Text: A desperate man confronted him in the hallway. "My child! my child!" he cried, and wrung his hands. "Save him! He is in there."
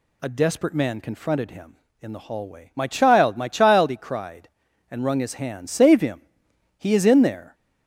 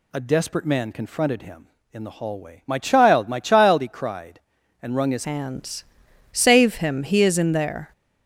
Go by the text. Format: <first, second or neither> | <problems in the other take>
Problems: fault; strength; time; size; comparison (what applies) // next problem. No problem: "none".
first | changes voice at "hands"; from 5.2 s on; 2.7 s long